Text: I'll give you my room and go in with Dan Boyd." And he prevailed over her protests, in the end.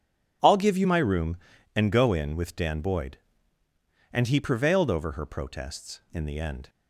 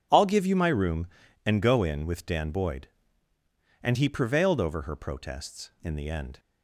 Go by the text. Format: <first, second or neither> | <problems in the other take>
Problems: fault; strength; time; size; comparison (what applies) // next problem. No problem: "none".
neither | none